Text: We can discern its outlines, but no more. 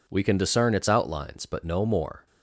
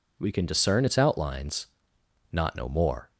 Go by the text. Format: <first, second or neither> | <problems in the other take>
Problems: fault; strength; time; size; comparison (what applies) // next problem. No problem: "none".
first | says "not" for "but"; at 2.3 s